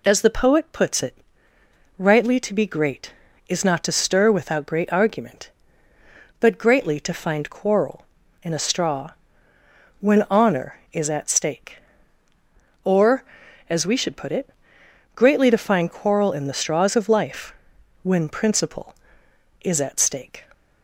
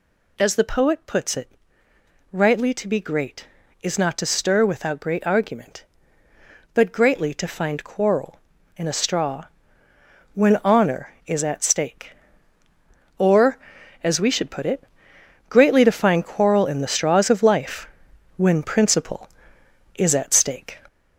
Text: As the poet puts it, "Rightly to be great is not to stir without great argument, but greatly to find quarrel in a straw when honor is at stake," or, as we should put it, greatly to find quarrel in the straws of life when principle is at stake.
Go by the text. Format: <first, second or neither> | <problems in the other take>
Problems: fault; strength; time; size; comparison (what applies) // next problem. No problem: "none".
first | gets louder; noticeable; throughout; 5 dB // pauses between "straw" and "when"; noticeable; at 9.4 s; 0.90 s long; noticeable in the first // pauses between "life" and "when"; noticeable; at 17.8 s; 0.50 s long; noticeable in the first